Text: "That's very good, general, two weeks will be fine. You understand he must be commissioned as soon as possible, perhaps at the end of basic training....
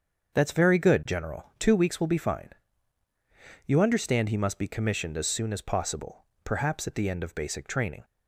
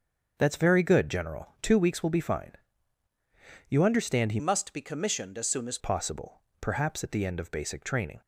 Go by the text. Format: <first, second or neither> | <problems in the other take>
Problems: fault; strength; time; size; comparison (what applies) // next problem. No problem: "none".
first | starts louder than the rest; until 1.3 s; 6.5 dB; also in the first // changes voice from "must" to "as"; from 4.3 to 5.7 s; 1.4 s long